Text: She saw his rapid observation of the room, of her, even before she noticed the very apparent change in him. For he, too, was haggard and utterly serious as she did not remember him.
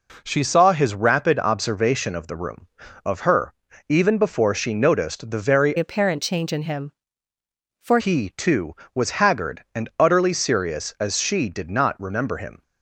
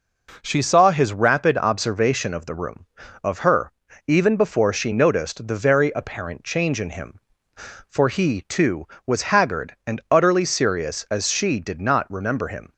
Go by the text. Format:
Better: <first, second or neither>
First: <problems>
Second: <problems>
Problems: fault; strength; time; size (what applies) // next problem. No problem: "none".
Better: second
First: changes voice from "apparent" to "For"; from 5.7 to 7.9 s; 2.2 s long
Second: none